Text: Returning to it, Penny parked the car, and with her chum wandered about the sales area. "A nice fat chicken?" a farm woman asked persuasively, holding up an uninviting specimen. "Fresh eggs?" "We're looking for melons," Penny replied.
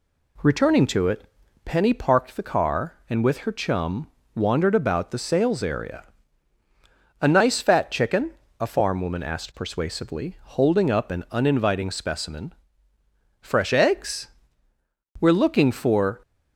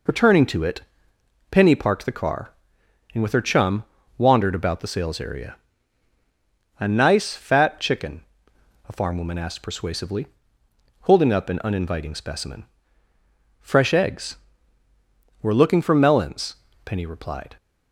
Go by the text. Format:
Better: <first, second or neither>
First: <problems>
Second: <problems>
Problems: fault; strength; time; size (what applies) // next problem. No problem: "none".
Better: second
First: pauses between "chum" and "wandered"; slight; at 4.0 s; 0.26 s long // stops before "melons Penny replied"; at 16.2 s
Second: pauses between "chum" and "wandered"; slight; at 3.8 s; 0.34 s long